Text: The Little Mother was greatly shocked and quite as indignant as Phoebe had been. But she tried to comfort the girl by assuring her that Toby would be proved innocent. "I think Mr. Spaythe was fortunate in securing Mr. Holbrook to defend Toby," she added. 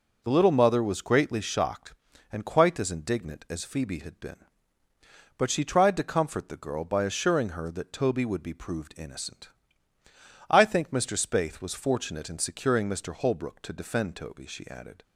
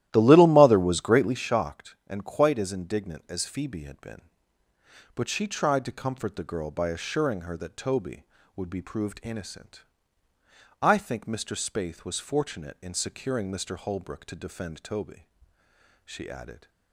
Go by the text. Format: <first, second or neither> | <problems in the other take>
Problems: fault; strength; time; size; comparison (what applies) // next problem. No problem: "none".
first | starts louder than the rest; strong; until 1.4 s; 13.5 dB